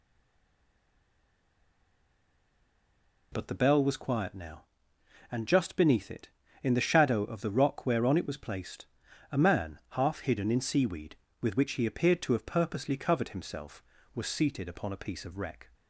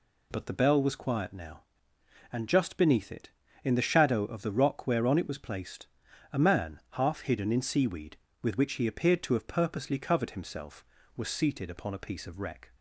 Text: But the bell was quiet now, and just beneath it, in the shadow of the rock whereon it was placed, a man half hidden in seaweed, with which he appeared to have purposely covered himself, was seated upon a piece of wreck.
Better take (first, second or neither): second